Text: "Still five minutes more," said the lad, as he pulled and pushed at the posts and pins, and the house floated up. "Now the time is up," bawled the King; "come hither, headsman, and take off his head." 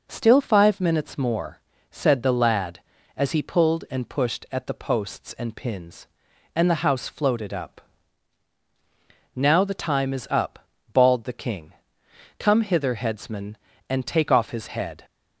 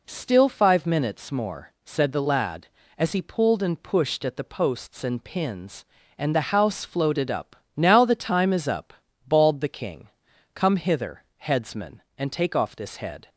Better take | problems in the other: first | says "this" for "his"; at 12.7 s

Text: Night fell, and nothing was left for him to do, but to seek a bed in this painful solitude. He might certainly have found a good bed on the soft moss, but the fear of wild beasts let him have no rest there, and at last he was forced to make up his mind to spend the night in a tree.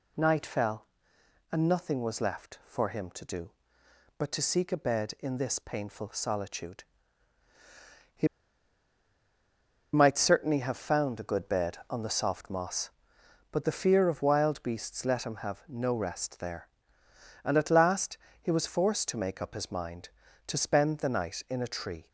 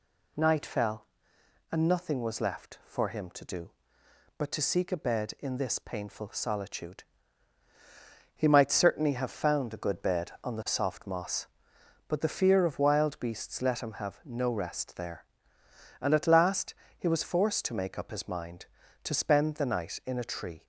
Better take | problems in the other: second | pauses between "He" and "might"; strong; at 8.2 s; 1.6 s long // pauses between "last" and "he"; slight; at 18.1 s; 0.24 s long; slight in the second

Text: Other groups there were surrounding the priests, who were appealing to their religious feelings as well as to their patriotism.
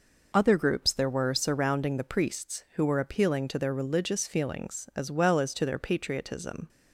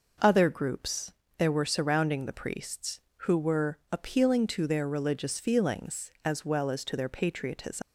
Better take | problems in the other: first | pauses between "groups" and "there"; slight; at 1.1 s; 0.24 s long // pauses between "were" and "appealing"; slight; at 3.7 s; 0.16 s long // leaves "patriotism" unfinished; at 7.8 s; 190 ms

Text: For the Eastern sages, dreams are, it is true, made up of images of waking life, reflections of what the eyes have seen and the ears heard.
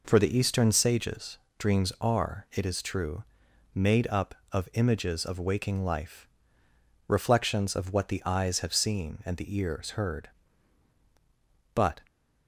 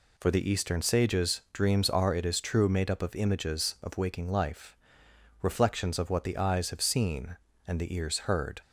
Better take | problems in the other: second | goes on to say "But"; slight; from 11.7 s on; 0.32 s long

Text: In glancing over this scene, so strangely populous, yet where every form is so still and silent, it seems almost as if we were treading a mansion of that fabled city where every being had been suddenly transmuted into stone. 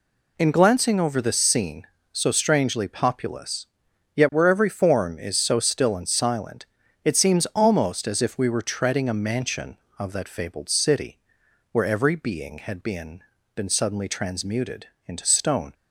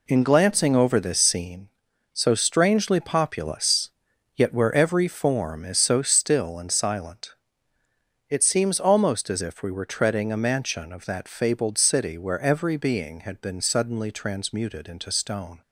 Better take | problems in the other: second | pauses between "city" and "where"; noticeable; at 11.1 s; 0.54 s long // says "been" twice; at 13.5 s // pauses between "transmuted" and "into"; slight; at 14.8 s; 0.22 s long

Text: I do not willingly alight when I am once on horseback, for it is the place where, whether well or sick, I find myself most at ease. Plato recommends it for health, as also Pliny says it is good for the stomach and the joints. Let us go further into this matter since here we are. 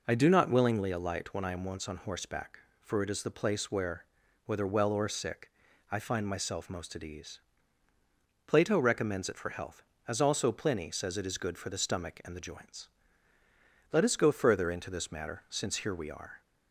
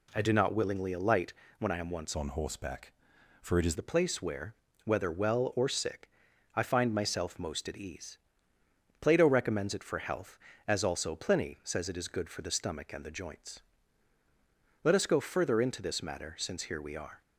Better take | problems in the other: first | pauses between "alight" and "when"; slight; at 1.3 s; 0.26 s long // changes voice from "on" to "is"; from 2.1 to 3.7 s; 1.6 s long

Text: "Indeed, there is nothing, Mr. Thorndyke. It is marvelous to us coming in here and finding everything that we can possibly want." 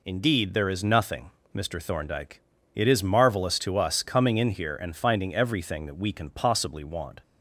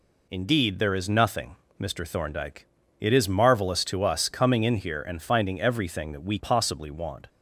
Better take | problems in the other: first | skips "can"; at 6.3 s

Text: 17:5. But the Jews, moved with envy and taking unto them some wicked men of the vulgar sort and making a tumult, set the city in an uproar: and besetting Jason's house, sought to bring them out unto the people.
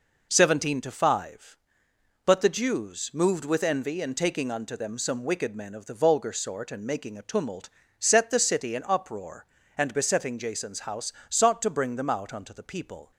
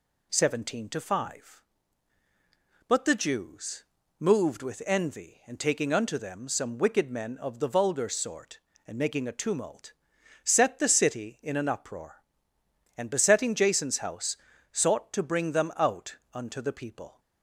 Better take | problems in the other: second | skips "an"; at 8.8 s

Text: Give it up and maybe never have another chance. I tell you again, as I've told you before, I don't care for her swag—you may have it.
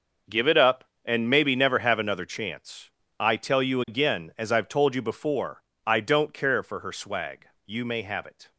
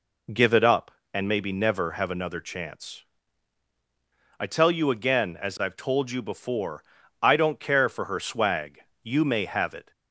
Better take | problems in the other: second | gets quieter; strong; throughout; 13 dB

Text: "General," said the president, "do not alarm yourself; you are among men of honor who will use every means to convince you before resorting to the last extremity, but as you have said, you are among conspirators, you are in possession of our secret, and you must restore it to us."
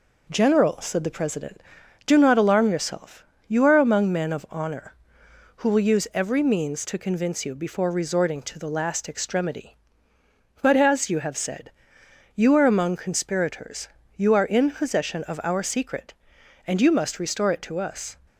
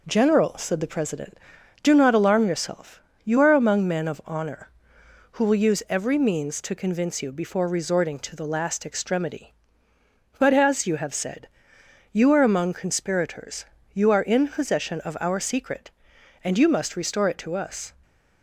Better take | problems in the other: neither | none

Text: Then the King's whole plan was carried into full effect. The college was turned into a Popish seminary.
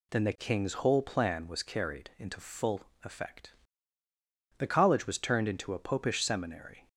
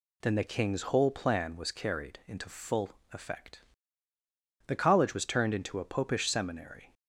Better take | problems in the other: neither | pauses between "full" and "effect"; slight; the same in both

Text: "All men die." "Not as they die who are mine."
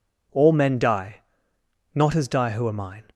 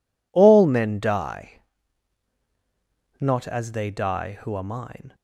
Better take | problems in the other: second | skips "they"; at 2.2 s

